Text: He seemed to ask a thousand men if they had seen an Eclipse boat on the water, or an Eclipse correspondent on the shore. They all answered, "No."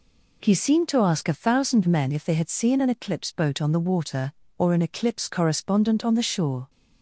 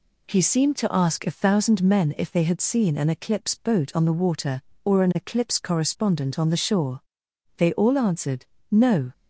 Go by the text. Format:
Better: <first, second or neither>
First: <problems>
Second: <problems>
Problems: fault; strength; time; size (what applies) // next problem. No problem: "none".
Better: second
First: stops before "They all answered No"; at 6.6 s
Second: none